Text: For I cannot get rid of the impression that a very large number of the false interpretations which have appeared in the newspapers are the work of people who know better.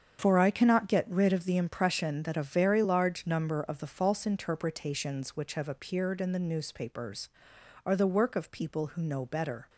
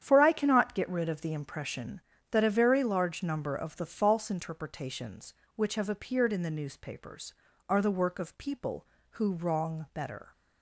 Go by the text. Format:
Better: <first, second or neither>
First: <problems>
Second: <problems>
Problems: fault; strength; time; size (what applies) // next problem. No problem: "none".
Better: first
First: starts louder than the rest; strong; until 1.2 s; 7.5 dB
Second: starts louder than the rest; strong; until 1.0 s; 9 dB // says "wrong" for "know"; at 9.3 s